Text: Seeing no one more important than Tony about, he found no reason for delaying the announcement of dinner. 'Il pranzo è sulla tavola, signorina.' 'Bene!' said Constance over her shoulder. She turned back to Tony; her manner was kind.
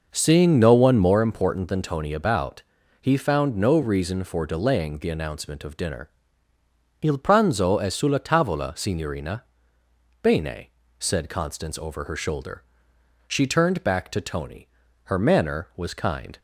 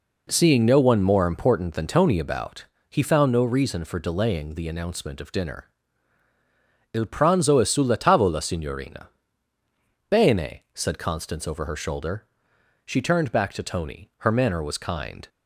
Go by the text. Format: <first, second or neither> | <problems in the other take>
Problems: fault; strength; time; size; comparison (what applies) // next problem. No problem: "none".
second | starts louder than the rest; noticeable; until 1.3 s; 6 dB